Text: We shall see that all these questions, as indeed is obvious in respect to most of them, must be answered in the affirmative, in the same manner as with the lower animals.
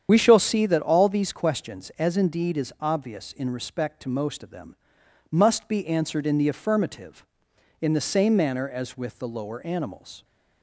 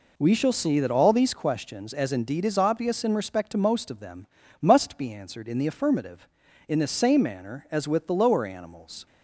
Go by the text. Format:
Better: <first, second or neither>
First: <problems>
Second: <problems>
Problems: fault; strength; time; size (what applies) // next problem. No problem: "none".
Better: second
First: loses the start of "We"; at 0.0 s; 35 ms // starts louder than the rest; strong; until 1.1 s; 8.5 dB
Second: none